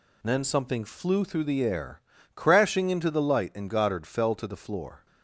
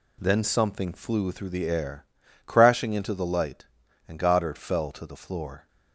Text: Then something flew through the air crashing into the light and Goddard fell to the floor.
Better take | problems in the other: neither | pauses between "air" and "crashing"; the same in both

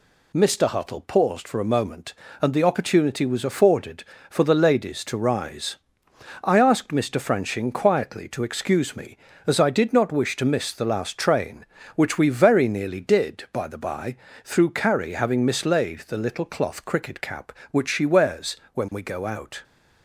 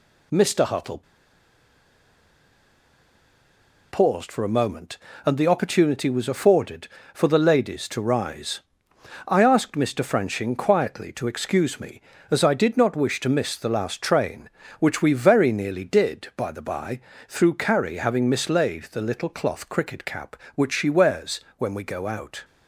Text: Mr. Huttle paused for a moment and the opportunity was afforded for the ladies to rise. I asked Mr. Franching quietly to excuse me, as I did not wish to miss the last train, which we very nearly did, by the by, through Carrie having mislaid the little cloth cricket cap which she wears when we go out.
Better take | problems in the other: first | pauses between "Huttle" and "paused"; strong; at 1.0 s; 2.8 s long // pauses between "wears" and "when"; slight; at 21.4 s; 0.18 s long; slight in the first

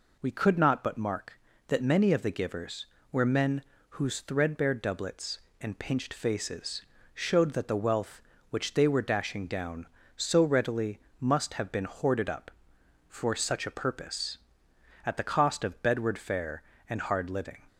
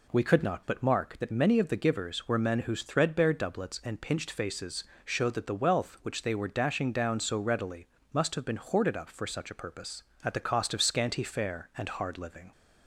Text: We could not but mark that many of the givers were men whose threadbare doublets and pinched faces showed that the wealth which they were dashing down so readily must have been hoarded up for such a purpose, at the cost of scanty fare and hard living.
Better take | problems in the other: second | pauses between "men" and "whose"; slight; at 3.6 s; 0.28 s long // pauses between "faces" and "showed"; slight; at 6.8 s; 0.32 s long; slight in the second // pauses between "readily" and "must"; slight; at 10.9 s; 0.20 s long; slight in the second // says "bedward" for "scanty"; at 15.8 s

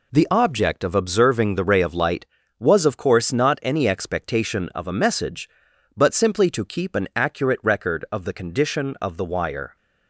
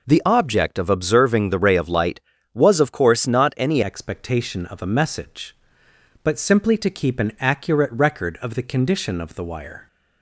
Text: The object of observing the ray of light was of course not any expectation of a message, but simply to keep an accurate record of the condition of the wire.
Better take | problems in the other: first | changes voice at "expectation"; from 3.8 s on; 6.0 s long

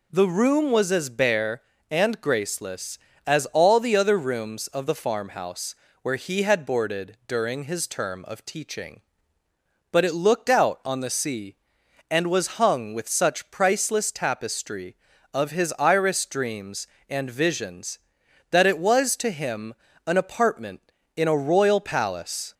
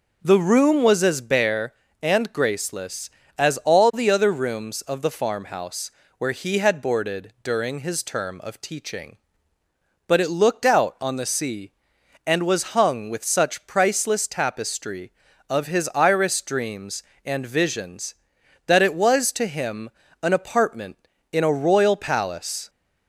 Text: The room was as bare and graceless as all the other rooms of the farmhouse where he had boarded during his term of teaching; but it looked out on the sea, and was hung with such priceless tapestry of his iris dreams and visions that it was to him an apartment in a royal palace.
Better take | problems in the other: first | starts louder than the rest; noticeable; until 1.3 s; 5.5 dB // pauses between "farmhouse" and "where"; slight; at 5.9 s; 0.26 s long; slight in the first // pauses between "him" and "an"; slight; at 19.8 s; 0.32 s long; slight in the first

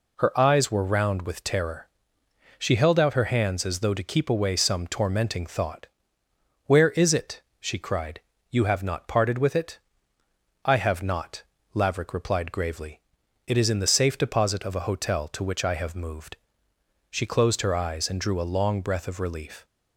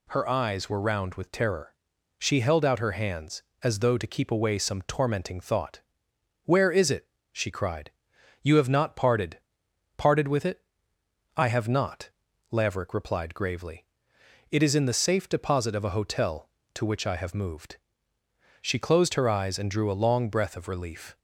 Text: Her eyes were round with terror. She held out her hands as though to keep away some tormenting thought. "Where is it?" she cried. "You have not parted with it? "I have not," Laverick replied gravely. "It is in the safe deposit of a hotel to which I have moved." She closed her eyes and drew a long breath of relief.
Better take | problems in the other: first | says "parted" twice; at 9.9 s

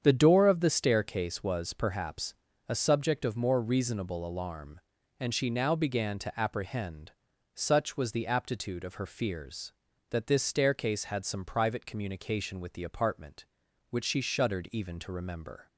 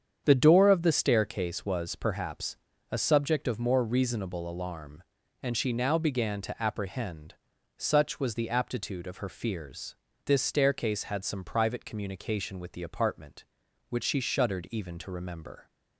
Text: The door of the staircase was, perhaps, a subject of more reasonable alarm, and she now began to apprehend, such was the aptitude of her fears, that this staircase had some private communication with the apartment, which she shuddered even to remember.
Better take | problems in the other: first | starts louder than the rest; strong; until 1.2 s; 8 dB; strong in the first // skips "that"; at 10.1 s

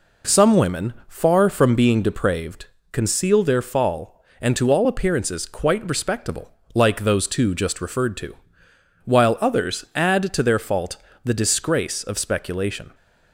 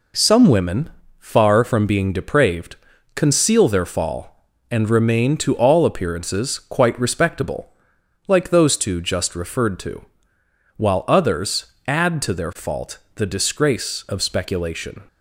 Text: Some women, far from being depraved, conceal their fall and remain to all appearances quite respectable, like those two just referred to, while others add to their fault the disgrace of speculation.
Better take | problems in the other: second | skips "remain"; at 4.5 s // pauses between "fault" and "the"; slight; at 10.9 s; 0.28 s long; slight in the second

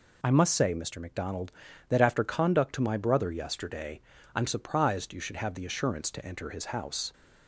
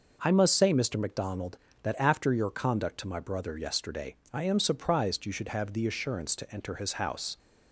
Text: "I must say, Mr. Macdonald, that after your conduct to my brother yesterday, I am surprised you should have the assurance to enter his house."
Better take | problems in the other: second | skips "your"; at 2.2 s

